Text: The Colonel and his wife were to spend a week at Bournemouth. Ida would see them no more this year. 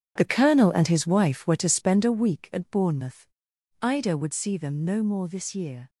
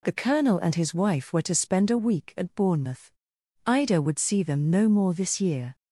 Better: second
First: gets quieter; strong; throughout; 11.5 dB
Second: none

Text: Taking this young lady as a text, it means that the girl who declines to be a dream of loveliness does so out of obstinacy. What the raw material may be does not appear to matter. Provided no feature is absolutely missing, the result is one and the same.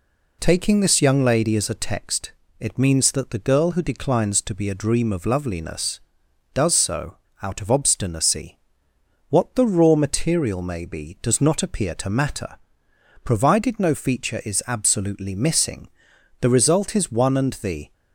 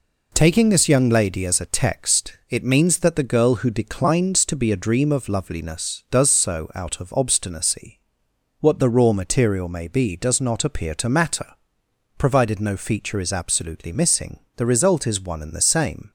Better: second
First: pauses between "so" and "out"; slight; at 7.1 s; 0.25 s long // stops before "same"; at 17.9 s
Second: none

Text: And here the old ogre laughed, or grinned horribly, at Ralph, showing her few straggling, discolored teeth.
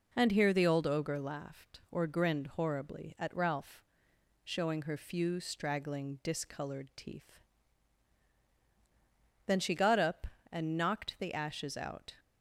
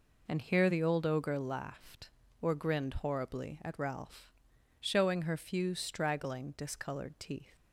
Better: second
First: goes on to say "Then she got up and knocked the ashes out"; strong; from 9.4 s on; 2.6 s long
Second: none

